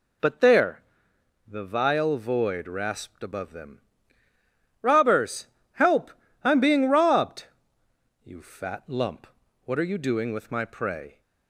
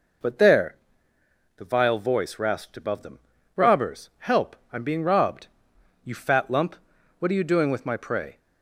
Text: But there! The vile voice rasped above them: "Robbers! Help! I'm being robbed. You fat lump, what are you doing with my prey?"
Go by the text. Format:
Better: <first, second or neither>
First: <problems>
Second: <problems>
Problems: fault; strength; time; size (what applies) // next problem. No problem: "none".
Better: second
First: says "void" for "voice"; at 2.1 s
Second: none